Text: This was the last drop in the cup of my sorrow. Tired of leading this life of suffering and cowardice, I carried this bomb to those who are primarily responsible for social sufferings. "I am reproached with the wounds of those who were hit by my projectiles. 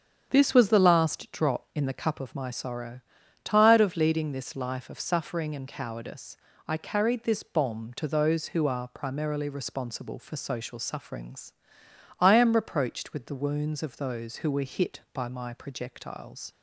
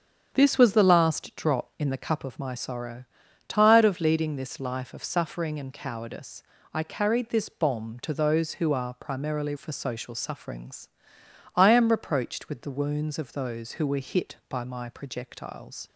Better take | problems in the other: first | starts louder than the rest; strong; until 1.3 s; 7.5 dB; strong in the first // skips "responsible"; at 9.5 s

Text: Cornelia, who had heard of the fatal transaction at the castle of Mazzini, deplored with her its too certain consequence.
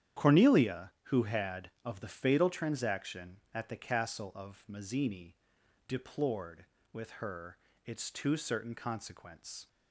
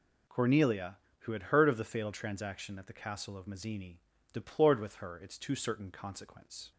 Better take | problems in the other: second | starts louder than the rest; strong; until 1.3 s; 10 dB // skips "heard"; at 1.7 s // pauses between "her" and "its"; slight; at 7.5 s; 0.28 s long

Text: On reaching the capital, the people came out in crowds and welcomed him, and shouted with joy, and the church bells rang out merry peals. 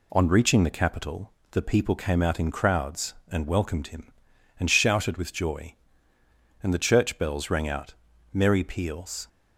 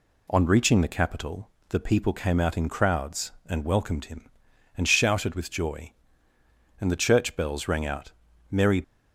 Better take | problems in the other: first | pauses between "out" and "merry"; at 8.1 s; 0.40 s long; also in the first // stops before "peals"; at 8.8 s

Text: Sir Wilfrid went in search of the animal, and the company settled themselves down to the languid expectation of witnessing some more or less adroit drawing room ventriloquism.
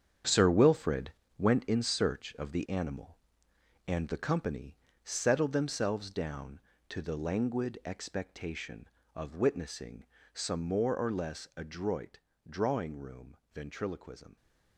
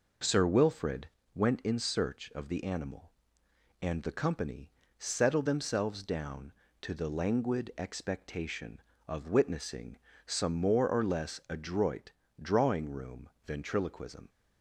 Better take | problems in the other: second | gets quieter; strong; throughout; 9.5 dB // pauses between "Wilfrid" and "went"; slight; at 1.1 s; 0.26 s long; slight in the second // pauses between "company" and "settled"; slight; at 4.7 s; 0.26 s long; slight in the second // pauses between "witnessing" and "some"; slight; at 10.0 s; 0.30 s long; slight in the second // pauses between "adroit" and "drawing"; slight; at 12.1 s; 0.28 s long; slight in the second // pauses between "room" and "ventriloquism"; slight; at 13.3 s; 0.16 s long; slight in the second

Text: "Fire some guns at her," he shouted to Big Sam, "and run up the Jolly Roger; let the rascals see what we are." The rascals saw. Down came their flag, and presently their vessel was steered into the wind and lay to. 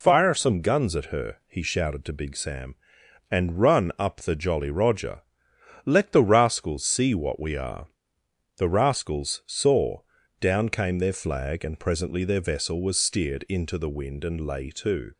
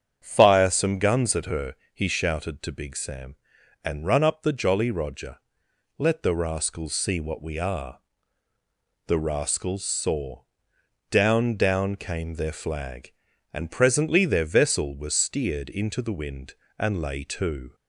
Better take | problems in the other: first | starts louder than the rest; strong; until 1.2 s; 8 dB // says "Down" twice; at 11.5 s

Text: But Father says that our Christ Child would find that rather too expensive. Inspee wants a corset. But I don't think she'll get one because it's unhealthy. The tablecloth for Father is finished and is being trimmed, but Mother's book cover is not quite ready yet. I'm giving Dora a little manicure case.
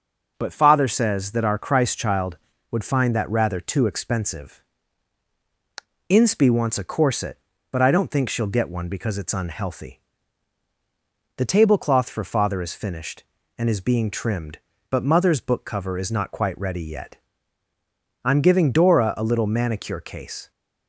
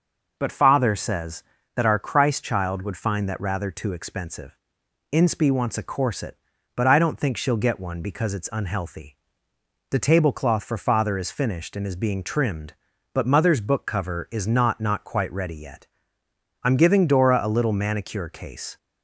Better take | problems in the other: first | says "not" twice; at 14.8 s

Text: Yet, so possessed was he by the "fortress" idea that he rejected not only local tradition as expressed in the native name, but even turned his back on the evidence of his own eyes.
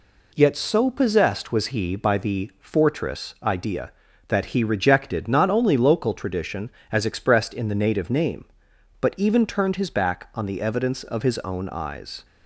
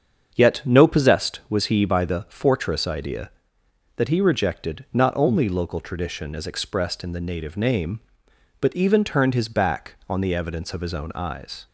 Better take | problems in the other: first | starts louder than the rest; until 1.3 s; 7 dB // says "no" for "so"; at 0.6 s

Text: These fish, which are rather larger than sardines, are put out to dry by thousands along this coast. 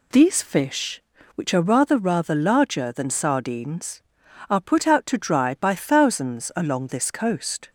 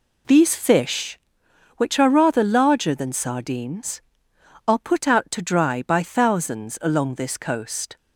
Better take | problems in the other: second | says "rather" twice; at 1.9 s

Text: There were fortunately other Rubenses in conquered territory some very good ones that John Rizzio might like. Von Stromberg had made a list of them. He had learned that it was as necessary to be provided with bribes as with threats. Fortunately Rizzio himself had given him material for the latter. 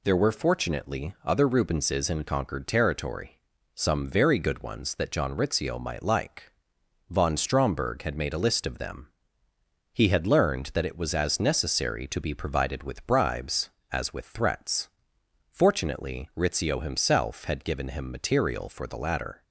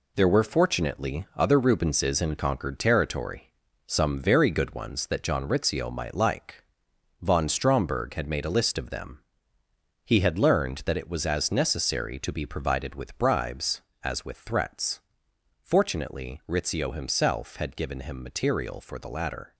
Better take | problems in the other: first | gets quieter; strong; throughout; 7 dB // pauses between "territory" and "some"; at 3.4 s; 0.40 s long; also in the first

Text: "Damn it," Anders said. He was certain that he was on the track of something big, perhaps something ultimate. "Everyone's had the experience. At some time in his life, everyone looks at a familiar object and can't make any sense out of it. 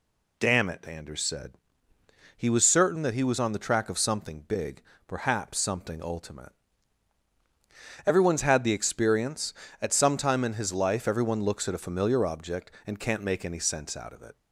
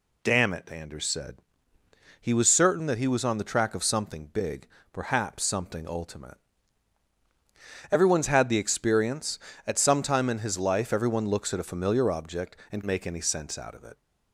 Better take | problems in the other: first | skips "can't"; at 12.8 s

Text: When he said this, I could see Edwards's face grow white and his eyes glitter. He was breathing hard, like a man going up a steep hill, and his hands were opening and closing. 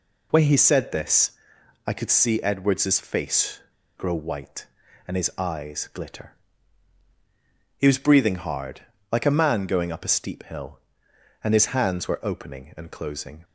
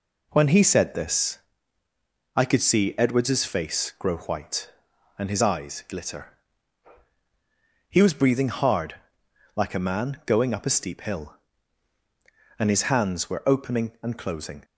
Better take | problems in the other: second | pauses between "face" and "grow"; at 3.5 s; 0.39 s long

